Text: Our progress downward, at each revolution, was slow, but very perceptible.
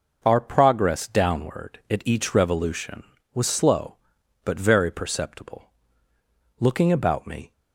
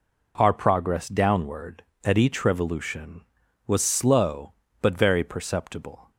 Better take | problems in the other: second | goes on to say "Looking about me"; noticeable; from 6.5 s on; 0.92 s long

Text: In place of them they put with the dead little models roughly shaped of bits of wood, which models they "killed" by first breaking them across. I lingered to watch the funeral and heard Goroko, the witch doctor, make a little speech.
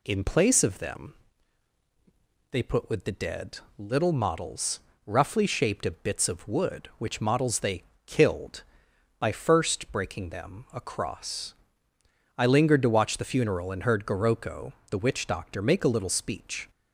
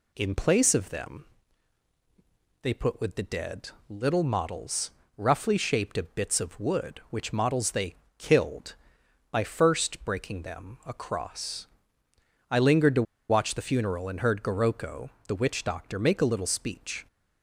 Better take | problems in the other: first | pauses between "them" and "they"; strong; at 1.2 s; 1.3 s long; strong in the first // pauses between "dead" and "little"; slight; at 3.7 s; 0.18 s long; slight in the first // pauses between "models" and "roughly"; slight; at 4.9 s; 0.26 s long; slight in the first // pauses between "they" and "killed"; slight; at 7.9 s; 0.24 s long; slight in the first // pauses between "to" and "watch"; slight; at 13.0 s; 0.27 s long

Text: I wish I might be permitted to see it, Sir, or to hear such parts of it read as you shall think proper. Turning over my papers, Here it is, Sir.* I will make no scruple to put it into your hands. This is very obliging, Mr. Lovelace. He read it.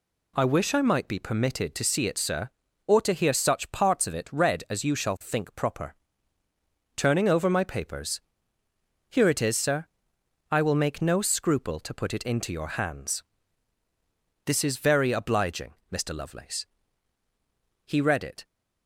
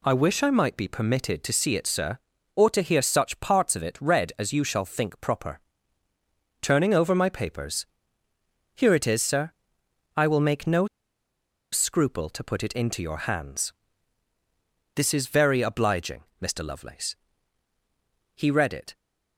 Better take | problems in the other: first | pauses between "no" and "scruple"; noticeable; at 10.8 s; 0.86 s long

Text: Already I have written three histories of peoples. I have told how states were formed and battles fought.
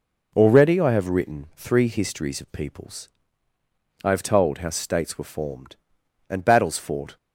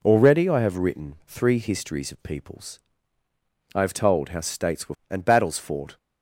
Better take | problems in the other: first | skips "formed"; at 5.0 s

